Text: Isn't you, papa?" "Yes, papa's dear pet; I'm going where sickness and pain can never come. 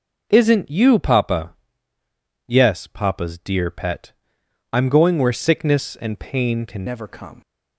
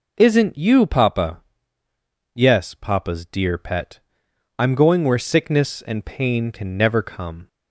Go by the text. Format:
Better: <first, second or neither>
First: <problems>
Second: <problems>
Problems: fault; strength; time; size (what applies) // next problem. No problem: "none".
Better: second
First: changes voice at "never"; from 6.8 s on; 0.6 s long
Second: none